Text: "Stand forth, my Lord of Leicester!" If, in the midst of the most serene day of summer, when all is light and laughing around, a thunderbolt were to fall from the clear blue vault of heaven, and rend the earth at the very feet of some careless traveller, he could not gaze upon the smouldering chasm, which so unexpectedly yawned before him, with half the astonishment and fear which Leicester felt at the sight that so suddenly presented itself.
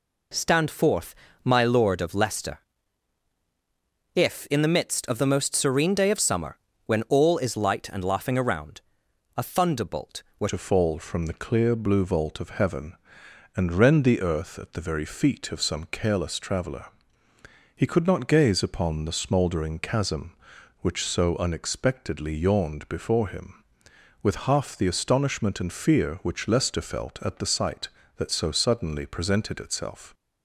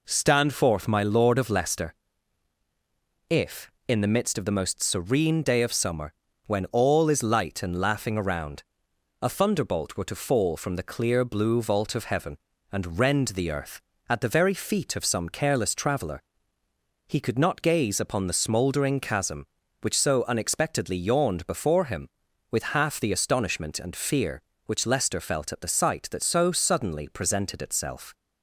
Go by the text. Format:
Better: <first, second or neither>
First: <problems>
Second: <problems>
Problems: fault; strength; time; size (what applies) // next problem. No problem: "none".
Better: second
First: changes voice at "to"; from 10.4 s on; 19.7 s long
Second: none